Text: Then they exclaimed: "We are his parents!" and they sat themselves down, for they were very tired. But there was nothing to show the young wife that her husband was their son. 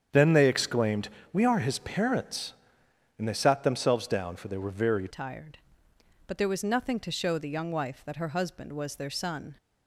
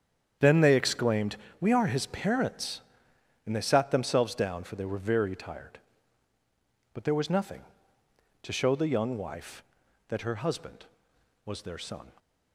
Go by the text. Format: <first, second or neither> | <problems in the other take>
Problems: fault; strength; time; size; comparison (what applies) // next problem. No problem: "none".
second | starts louder than the rest; strong; until 1.3 s; 8 dB; strong in the second // changes voice at "tired"; from 5.0 s on; 4.5 s long